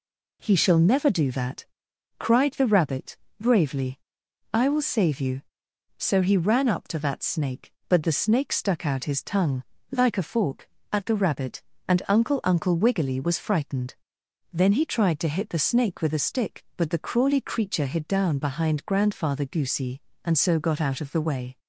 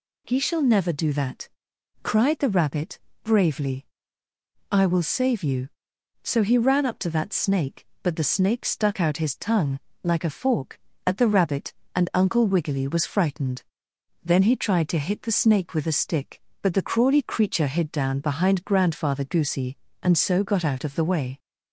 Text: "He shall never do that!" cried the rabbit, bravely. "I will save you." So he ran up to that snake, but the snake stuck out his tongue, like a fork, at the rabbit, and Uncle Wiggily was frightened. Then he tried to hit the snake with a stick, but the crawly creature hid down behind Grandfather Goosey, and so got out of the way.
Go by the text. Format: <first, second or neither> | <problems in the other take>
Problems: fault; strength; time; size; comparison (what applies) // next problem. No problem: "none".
second | says "Uncle" twice; at 12.4 s